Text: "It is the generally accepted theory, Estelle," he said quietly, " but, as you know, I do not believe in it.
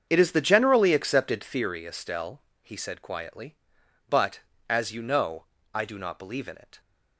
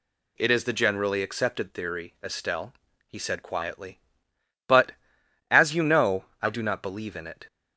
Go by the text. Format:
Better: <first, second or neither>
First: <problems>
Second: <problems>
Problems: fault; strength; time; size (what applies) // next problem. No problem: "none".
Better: second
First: starts louder than the rest; strong; until 1.6 s; 7.5 dB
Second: none